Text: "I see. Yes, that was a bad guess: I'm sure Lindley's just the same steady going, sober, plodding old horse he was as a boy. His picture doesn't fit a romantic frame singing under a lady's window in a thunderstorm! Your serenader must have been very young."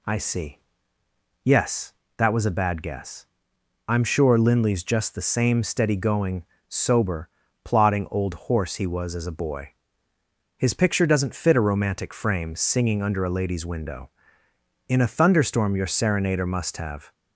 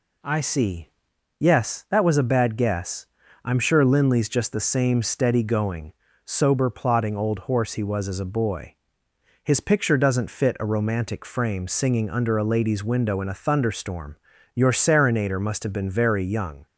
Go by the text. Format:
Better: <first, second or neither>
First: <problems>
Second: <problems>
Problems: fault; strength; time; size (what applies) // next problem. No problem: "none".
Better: second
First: stops before "been very young"; at 17.1 s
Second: none